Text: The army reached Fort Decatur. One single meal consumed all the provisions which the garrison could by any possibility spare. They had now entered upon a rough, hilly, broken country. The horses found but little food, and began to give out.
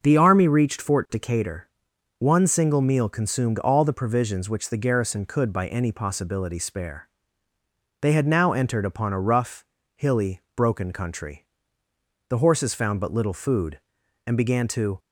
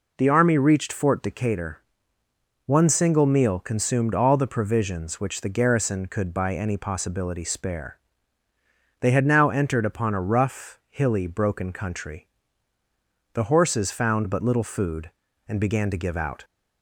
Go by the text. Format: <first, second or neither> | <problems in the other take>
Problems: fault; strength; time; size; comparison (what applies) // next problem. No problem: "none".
second | starts louder than the rest; until 1.0 s; 6 dB // stops before "give out"; at 14.9 s